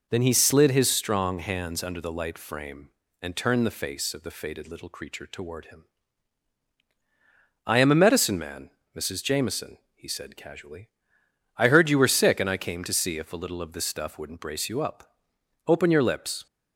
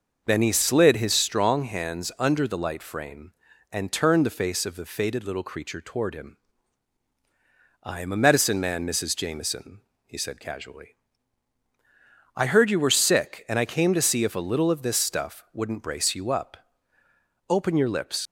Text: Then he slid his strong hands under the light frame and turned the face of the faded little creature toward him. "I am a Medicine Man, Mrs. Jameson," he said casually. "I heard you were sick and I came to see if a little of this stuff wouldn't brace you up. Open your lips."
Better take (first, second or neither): first